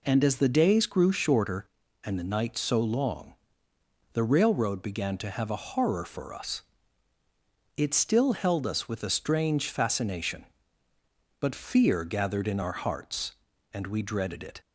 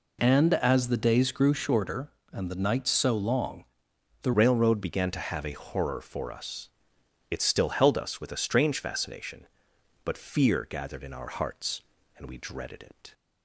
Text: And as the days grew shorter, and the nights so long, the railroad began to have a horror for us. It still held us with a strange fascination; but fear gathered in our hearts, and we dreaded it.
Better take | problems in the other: first | changes voice at "railroad"; from 4.3 s on; 8.8 s long

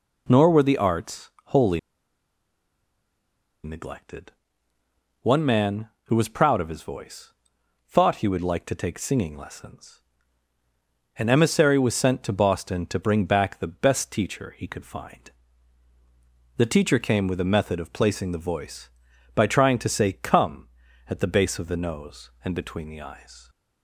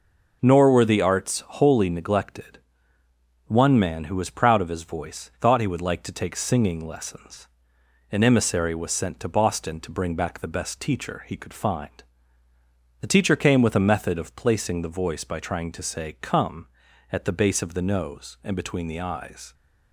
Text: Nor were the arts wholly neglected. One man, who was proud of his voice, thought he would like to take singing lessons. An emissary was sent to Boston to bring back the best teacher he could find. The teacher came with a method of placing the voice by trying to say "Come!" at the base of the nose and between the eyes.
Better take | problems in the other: second | pauses between "arts" and "wholly"; slight; at 1.2 s; 0.16 s long // pauses between "wholly" and "neglected"; strong; at 1.7 s; 1.8 s long

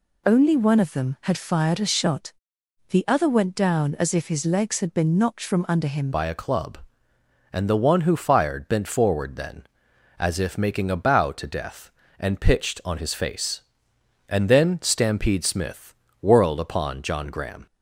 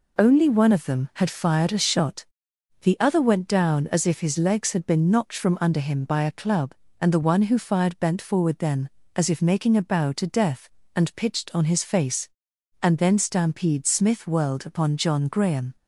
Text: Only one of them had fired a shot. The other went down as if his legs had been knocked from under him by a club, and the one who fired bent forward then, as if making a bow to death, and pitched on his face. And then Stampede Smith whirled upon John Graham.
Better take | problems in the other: second | changes voice at "by"; from 6.1 s on; 11.5 s long // pauses between "Smith" and "whirled"; slight; at 15.9 s; 0.26 s long

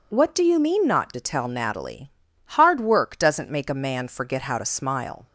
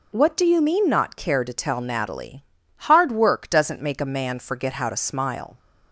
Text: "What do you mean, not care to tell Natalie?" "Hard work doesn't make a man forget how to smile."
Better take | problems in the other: second | skips "care"; at 1.1 s

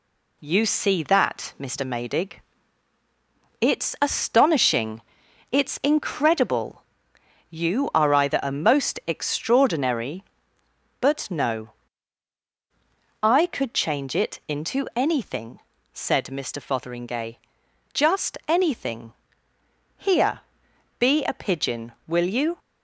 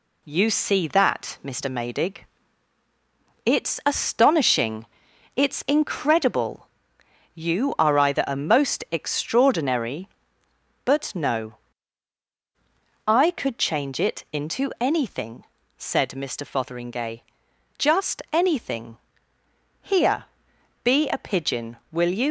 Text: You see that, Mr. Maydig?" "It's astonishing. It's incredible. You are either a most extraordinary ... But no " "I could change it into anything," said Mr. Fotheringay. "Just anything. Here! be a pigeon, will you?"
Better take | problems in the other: first | leaves "you" unfinished; at 22.2 s; 125 ms

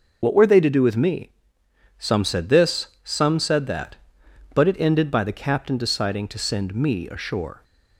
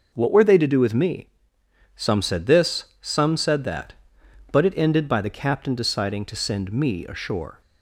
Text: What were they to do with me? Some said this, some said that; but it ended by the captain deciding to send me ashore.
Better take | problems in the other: second | loses the start of "What"; at 0.2 s; 60 ms // starts louder than the rest; until 1.2 s; 6.5 dB

